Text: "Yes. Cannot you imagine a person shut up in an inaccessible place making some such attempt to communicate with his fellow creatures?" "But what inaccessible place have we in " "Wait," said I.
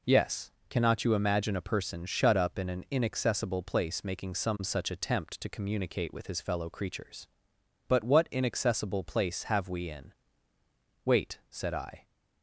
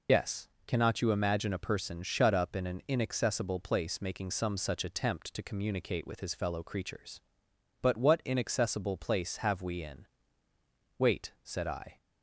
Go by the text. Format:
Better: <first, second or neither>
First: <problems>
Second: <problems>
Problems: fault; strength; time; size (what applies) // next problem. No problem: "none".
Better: first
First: none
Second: loses the start of "Yes"; at 0.0 s; 70 ms